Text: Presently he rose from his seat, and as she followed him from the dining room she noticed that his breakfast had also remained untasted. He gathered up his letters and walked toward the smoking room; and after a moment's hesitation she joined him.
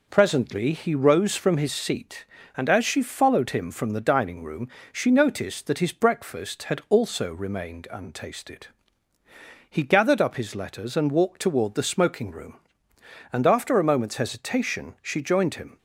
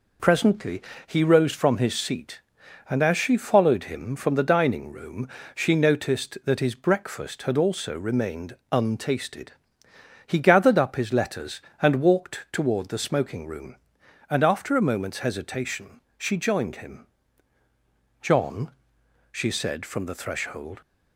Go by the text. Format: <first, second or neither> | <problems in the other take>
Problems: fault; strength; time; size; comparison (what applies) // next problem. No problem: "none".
first | pauses between "Presently" and "he"; slight; at 0.8 s; 0.24 s long // pauses between "room" and "she"; slight; at 5.2 s; 0.28 s long; slight in the first // pauses between "remained" and "untasted"; slight; at 8.5 s; 0.16 s long // pauses between "hesitation" and "she"; slight; at 16.0 s; 0.18 s long // goes on to say "John she said from the threshold"; strong; from 18.2 s on; 2.6 s long